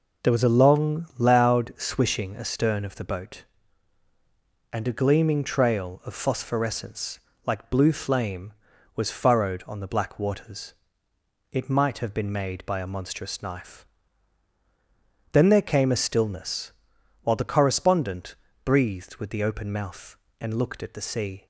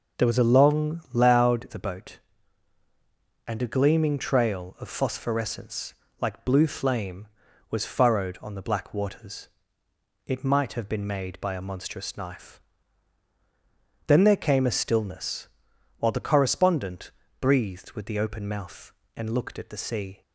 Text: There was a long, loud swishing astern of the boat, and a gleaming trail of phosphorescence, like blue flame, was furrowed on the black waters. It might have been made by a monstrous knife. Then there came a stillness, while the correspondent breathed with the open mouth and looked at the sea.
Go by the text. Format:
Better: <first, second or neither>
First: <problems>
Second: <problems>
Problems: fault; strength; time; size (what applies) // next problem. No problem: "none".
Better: first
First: pauses between "correspondent" and "breathed"; slight; at 18.3 s; 0.30 s long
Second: starts louder than the rest; until 1.2 s; 6.5 dB // skips "swishing astern of"; at 1.6 s // pauses between "correspondent" and "breathed"; slight; at 17.1 s; 0.30 s long